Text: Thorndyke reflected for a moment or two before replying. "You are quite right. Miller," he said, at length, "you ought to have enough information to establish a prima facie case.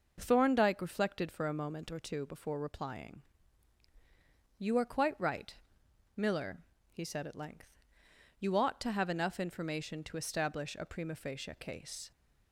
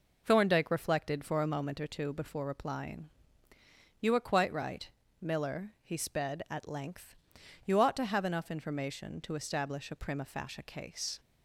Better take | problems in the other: first | says "sped" for "said"; at 5.9 s

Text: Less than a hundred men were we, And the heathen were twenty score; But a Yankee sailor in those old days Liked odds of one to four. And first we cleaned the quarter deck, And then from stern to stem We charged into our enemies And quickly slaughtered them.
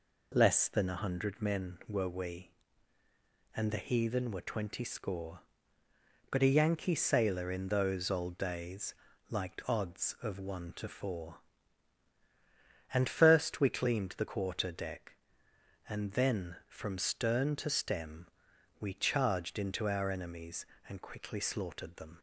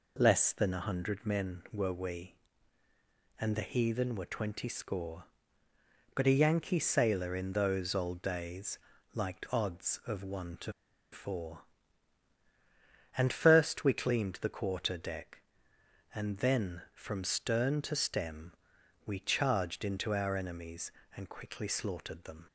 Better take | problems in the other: first | pauses between "days" and "Liked"; slight; at 8.7 s; 0.34 s long; slight in the first // pauses between "to" and "four"; at 10.7 s; 0.40 s long // pauses between "stem" and "We"; noticeable; at 18.5 s; 0.52 s long; noticeable in the first

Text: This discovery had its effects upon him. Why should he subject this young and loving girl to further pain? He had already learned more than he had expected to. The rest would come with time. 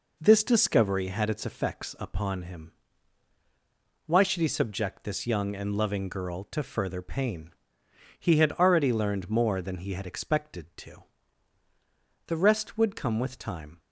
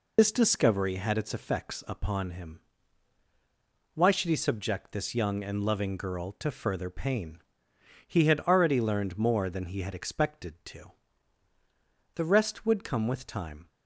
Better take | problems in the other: first | loses the start of "This"; at 0.1 s; 110 ms

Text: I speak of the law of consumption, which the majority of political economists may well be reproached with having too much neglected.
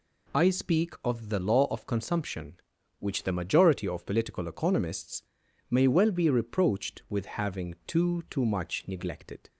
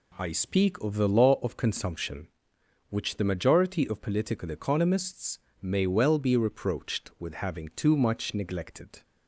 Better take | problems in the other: second | pauses between "economists" and "may"; noticeable; at 5.2 s; 0.48 s long; slight in the second // says "too" twice; at 8.2 s

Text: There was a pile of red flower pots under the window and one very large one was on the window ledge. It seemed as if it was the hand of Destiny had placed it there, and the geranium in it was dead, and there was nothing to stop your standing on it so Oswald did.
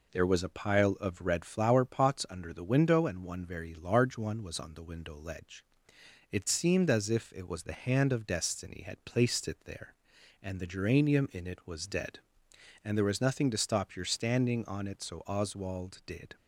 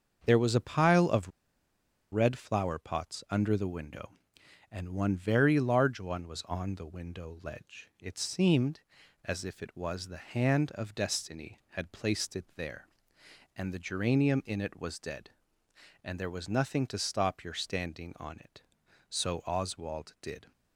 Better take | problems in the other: first | starts louder than the rest; until 1.2 s; 7 dB // pauses between "of" and "red"; noticeable; at 1.3 s; 0.81 s long

